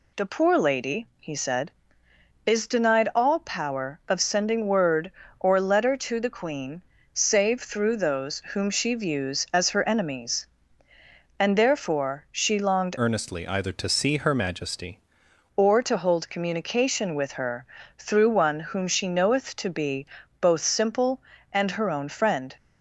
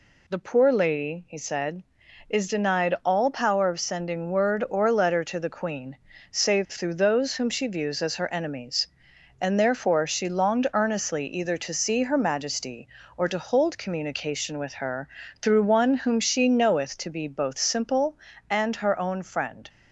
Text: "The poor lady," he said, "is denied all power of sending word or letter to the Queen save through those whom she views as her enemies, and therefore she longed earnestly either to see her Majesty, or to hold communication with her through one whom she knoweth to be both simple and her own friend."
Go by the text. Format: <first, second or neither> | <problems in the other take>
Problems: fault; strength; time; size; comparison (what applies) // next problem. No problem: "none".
second | pauses between "Queen" and "save"; slight; at 6.8 s; 0.30 s long; slight in the second // pauses between "those" and "whom"; slight; at 8.3 s; 0.16 s long // changes voice from "earnestly" to "Majesty"; from 12.9 to 14.9 s; 2.0 s long // pauses between "her" and "through"; slight; at 17.6 s; 0.32 s long; slight in the second // pauses between "be" and "both"; slight; at 20.0 s; 0.34 s long